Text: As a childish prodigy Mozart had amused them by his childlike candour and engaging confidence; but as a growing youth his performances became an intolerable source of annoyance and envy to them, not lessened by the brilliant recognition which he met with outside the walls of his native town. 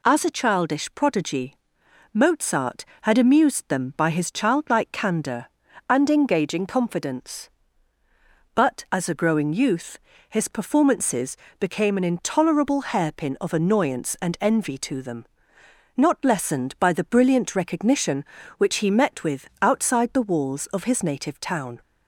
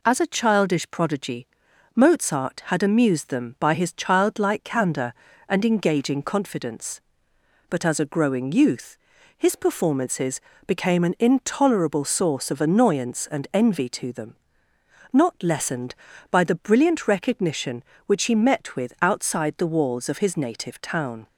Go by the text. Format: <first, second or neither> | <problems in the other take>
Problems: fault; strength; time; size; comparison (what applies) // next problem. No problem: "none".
second | pauses between "prodigy" and "Mozart"; noticeable; at 1.5 s; 0.58 s long; noticeable in the second // pauses between "youth" and "his"; slight; at 9.9 s; 0.32 s long; also in the second // pauses between "performances" and "became"; slight; at 11.3 s; 0.24 s long; slight in the second // says "hairpin" for "source"; at 12.8 s